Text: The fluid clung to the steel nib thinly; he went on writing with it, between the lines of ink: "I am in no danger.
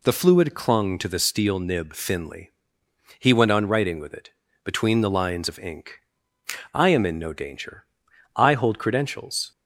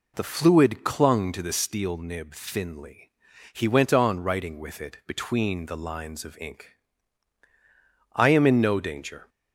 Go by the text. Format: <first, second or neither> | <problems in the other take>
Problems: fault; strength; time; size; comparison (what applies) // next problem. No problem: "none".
second | goes on to say "I hold credentials"; noticeable; from 8.3 s on; 1.1 s long